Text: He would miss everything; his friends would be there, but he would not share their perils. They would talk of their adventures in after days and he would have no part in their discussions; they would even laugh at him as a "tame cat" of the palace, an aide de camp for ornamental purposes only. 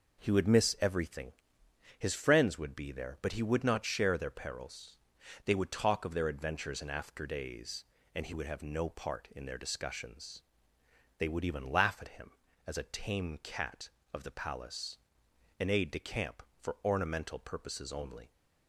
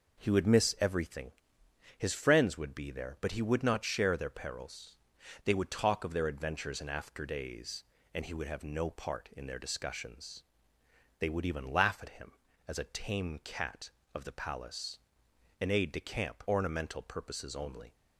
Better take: first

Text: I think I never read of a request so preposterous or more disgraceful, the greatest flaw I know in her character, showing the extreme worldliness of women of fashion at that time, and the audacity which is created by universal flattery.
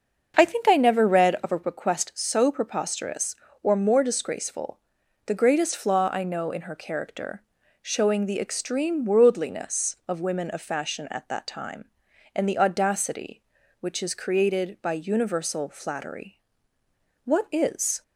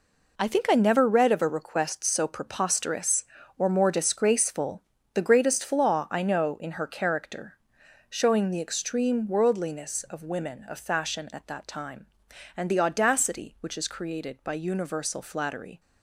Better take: second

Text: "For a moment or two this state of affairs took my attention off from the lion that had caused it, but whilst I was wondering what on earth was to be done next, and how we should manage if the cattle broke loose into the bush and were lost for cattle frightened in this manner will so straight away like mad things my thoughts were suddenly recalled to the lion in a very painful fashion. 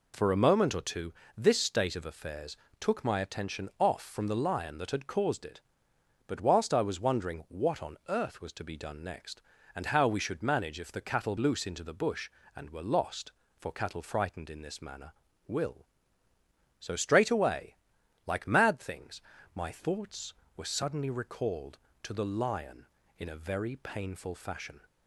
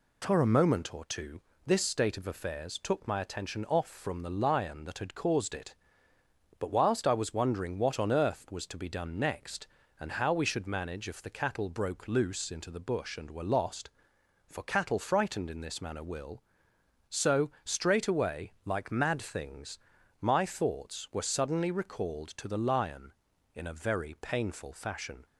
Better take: second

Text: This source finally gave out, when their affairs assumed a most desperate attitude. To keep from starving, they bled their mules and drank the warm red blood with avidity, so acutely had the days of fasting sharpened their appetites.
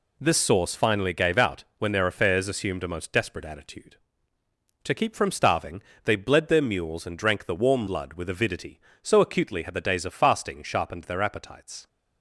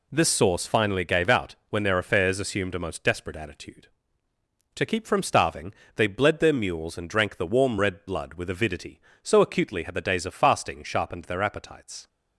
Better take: second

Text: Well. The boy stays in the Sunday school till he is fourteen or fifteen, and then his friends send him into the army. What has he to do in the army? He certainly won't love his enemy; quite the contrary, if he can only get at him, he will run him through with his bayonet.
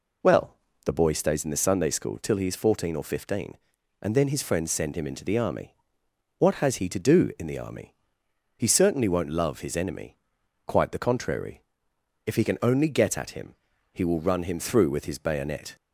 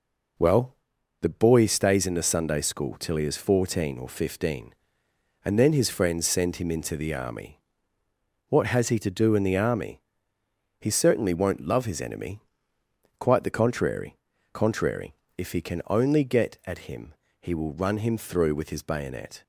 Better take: first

